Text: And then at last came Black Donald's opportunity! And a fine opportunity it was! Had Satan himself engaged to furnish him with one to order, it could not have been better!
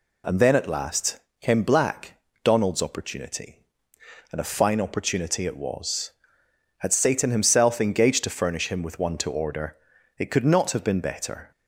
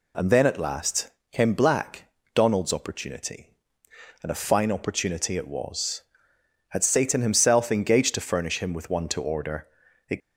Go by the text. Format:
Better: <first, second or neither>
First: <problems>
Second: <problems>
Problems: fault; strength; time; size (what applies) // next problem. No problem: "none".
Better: first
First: pauses between "last" and "came"; slight; at 1.1 s; 0.20 s long // pauses between "Black" and "Donald's"; slight; at 2.1 s; 0.26 s long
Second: pauses between "last" and "came"; slight; at 1.0 s; 0.20 s long // pauses between "Black" and "Donald's"; slight; at 2.0 s; 0.26 s long // stops before "could not have been better"; at 10.2 s